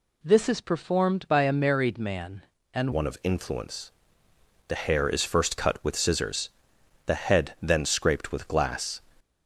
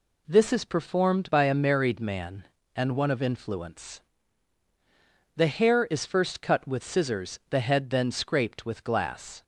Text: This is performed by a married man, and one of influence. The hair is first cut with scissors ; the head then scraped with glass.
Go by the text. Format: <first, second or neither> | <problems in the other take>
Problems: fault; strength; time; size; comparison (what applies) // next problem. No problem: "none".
second | changes voice at "one"; from 2.9 s on; 6.1 s long